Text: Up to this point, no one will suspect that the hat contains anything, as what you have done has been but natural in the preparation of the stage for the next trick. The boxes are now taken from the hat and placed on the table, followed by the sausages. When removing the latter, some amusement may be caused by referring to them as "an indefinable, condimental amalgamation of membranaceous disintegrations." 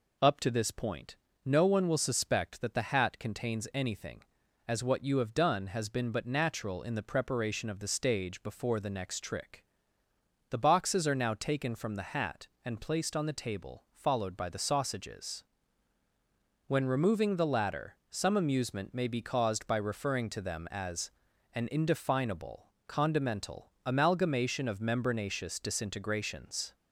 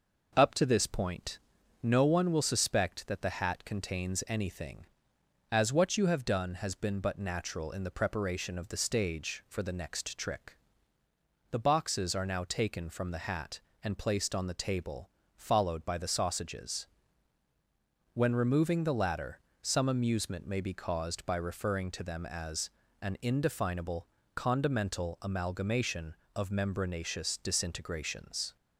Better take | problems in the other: second | says "before" for "for"; at 8.4 s // pauses between "as" and "an"; at 21.1 s; 0.42 s long; slight in the second // pauses between "condimental" and "amalgamation"; slight; at 23.6 s; 0.18 s long

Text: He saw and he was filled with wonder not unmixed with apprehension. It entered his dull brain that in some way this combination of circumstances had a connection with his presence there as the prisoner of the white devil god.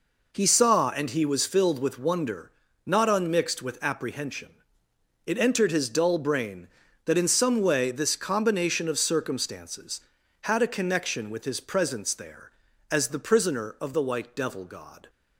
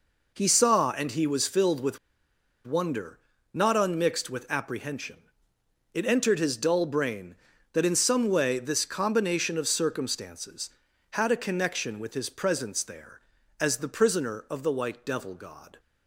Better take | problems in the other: first | pauses between "with" and "wonder"; noticeable; at 1.9 s; 0.68 s long // pauses between "wonder" and "not"; slight; at 3.1 s; 0.34 s long; slight in the first

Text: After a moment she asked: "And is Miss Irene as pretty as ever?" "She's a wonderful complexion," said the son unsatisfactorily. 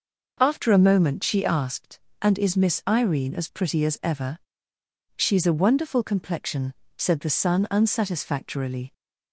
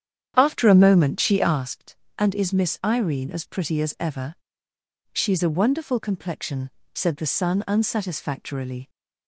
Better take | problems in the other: first | starts louder than the rest; strong; until 1.6 s; 9 dB

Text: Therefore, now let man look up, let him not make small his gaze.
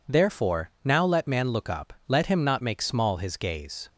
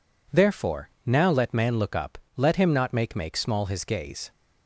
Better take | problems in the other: first | says "make" twice; at 3.1 s

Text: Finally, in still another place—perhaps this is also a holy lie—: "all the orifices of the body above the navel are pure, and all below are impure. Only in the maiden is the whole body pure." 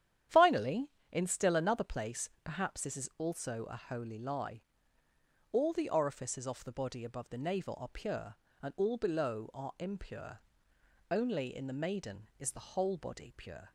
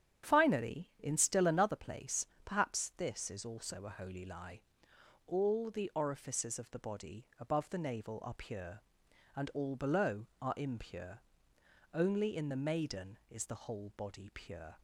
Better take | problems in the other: second | starts louder than the rest; strong; until 1.5 s; 10 dB; strong in the second // says "off" for "of"; at 6.4 s

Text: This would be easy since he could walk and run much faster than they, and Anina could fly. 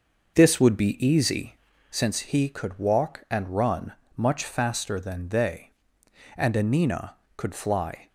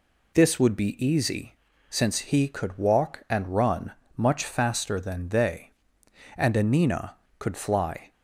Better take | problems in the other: second | starts louder than the rest; noticeable; until 2.0 s; 6 dB // pauses between "easy" and "since"; slight; at 1.5 s; 0.32 s long; slight in the second // pauses between "run" and "much"; slight; at 3.9 s; 0.25 s long; slight in the second

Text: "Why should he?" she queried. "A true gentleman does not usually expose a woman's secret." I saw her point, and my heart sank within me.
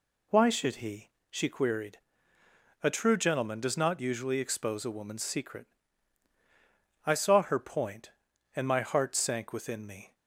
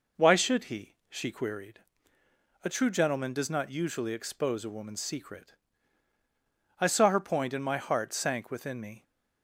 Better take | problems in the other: neither | none

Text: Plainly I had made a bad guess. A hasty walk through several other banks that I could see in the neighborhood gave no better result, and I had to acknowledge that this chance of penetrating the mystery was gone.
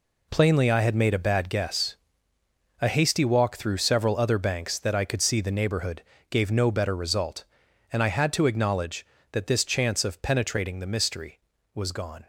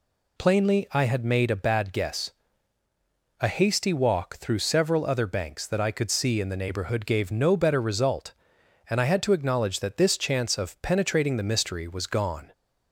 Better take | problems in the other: second | skips "in"; at 5.4 s // pauses between "neighborhood" and "gave"; slight; at 6.0 s; 0.28 s long

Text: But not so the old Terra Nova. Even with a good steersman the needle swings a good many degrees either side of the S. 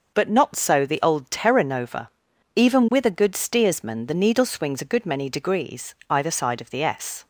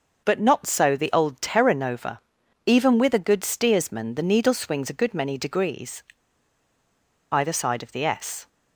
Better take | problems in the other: first | pauses between "degrees" and "either"; strong; at 6.0 s; 1.2 s long

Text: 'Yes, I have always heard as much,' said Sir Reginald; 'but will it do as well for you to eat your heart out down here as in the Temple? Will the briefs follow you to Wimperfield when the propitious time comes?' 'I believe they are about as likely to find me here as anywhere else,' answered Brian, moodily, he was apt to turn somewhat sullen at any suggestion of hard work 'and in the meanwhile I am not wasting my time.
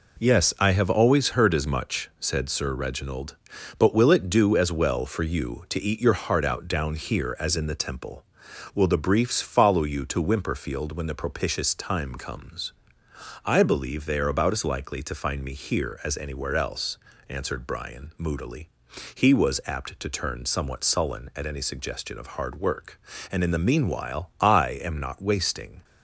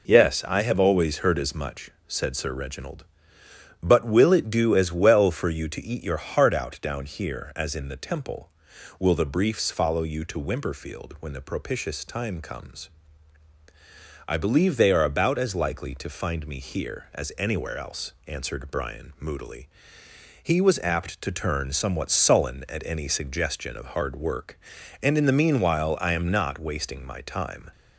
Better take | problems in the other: second | stops before "my time"; at 25.8 s

